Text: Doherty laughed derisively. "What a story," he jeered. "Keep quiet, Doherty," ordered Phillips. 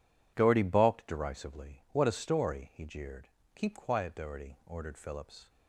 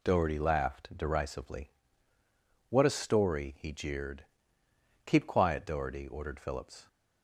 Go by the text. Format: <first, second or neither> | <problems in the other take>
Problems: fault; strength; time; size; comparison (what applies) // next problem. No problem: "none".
second | says "balked" for "laughed"; at 0.6 s